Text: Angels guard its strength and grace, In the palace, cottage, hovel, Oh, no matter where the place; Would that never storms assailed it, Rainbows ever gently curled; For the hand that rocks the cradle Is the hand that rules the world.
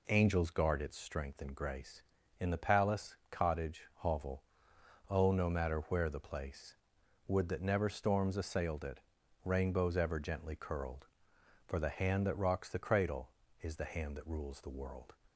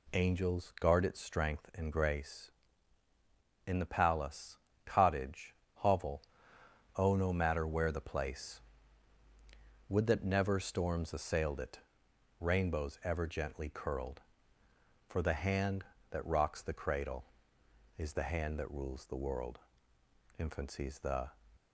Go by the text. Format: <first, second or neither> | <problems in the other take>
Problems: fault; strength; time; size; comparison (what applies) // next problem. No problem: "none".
first | goes on to say "Infancy's the"; noticeable; from 20.3 s on; 0.94 s long